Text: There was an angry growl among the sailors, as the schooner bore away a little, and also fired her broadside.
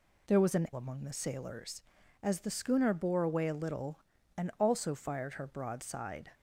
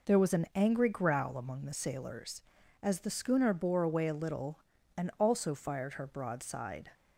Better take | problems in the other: second | skips "angry growl"; at 0.7 s

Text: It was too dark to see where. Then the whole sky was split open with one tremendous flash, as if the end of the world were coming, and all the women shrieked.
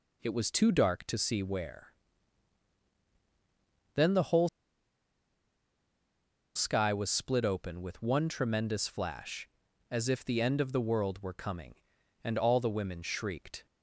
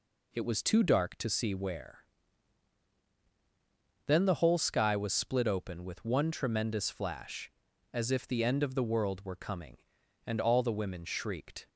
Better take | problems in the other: second | pauses between "whole" and "sky"; strong; at 4.4 s; 2.0 s long

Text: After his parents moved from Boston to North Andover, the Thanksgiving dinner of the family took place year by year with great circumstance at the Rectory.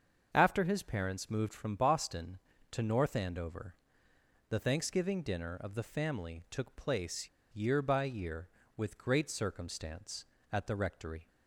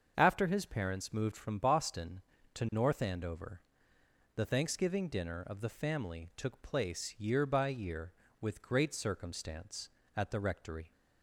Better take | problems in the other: second | starts louder than the rest; until 1.3 s; 7 dB; also in the second // pauses between "place" and "year"; slight; at 7.2 s; 0.26 s long

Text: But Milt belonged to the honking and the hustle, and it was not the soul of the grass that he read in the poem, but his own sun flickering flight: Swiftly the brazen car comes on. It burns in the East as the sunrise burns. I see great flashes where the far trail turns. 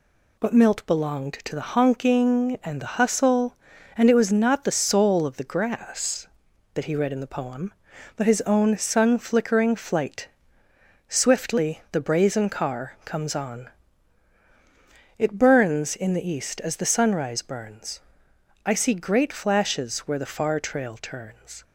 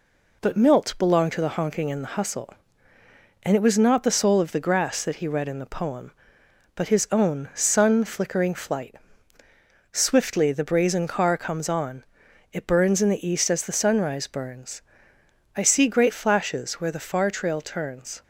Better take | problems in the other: neither | none

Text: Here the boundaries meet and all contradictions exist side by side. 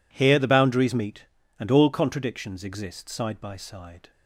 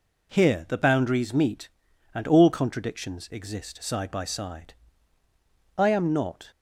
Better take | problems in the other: first | goes on to say "I am not"; noticeable; from 5.7 s on; 0.74 s long

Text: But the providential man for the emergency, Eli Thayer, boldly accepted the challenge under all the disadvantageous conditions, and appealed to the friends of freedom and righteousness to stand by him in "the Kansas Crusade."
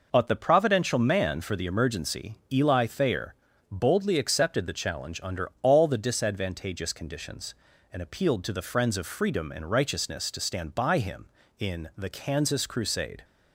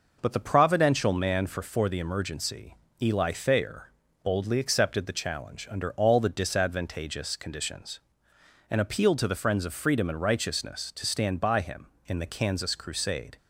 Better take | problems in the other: first | says "for" twice; at 1.6 s

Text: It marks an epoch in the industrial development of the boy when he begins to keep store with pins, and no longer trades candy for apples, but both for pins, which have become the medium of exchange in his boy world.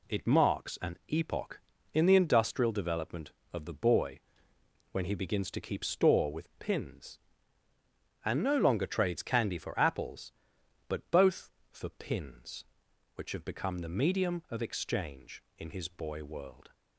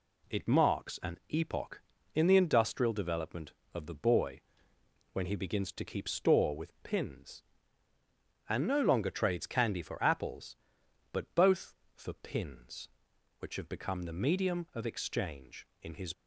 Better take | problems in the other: first | pauses between "boy" and "when"; noticeable; at 4.4 s; 0.72 s long; noticeable in the first // stops before "boy world"; at 16.1 s

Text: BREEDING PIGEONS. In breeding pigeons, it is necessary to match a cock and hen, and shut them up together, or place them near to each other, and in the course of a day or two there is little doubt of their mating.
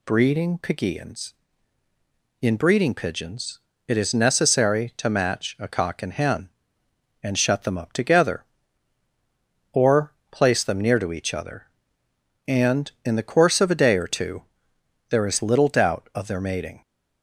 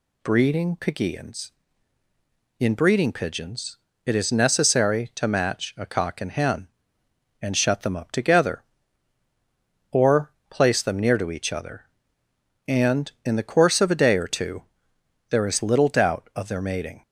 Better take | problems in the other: neither | pauses between "or" and "place"; slight; the same in both // pauses between "two" and "there"; noticeable; the same in both

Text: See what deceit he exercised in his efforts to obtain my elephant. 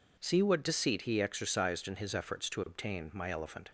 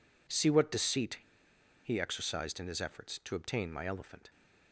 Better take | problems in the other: first | pauses between "deceit" and "he"; noticeable; at 1.1 s; 0.65 s long

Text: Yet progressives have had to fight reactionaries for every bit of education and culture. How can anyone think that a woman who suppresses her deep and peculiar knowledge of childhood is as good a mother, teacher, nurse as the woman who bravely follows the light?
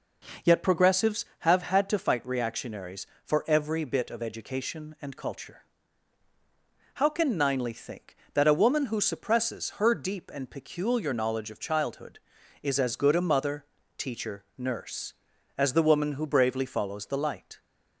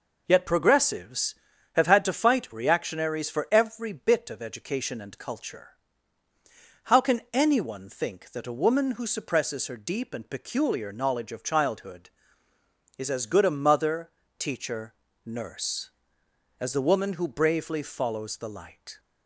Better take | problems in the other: second | says "ninely" for "anyone"; at 7.3 s

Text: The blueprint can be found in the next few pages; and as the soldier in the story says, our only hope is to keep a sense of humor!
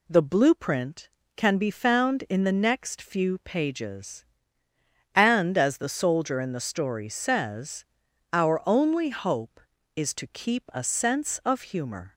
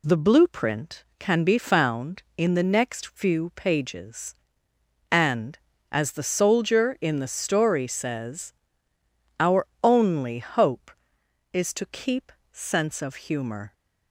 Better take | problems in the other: first | pauses between "our" and "only"; slight; at 9.6 s; 0.18 s long // skips "a"; at 12.4 s

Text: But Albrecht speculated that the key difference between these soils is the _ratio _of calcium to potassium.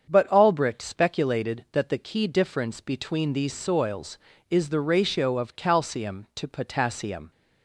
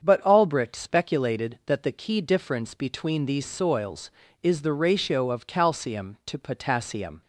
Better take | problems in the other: neither | starts louder than the rest; strong; the same in both

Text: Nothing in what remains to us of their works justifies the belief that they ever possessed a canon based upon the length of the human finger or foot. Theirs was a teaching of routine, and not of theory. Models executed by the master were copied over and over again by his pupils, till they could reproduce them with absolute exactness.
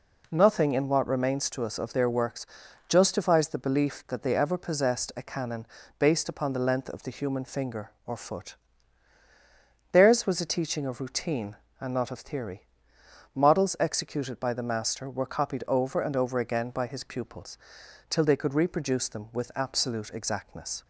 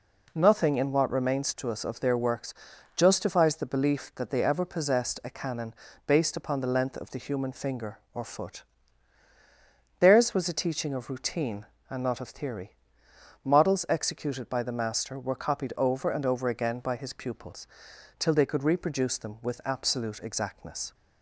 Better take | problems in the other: neither | pauses between "works" and "justifies"; the same in both // pauses between "canon" and "based"; slight; the same in both

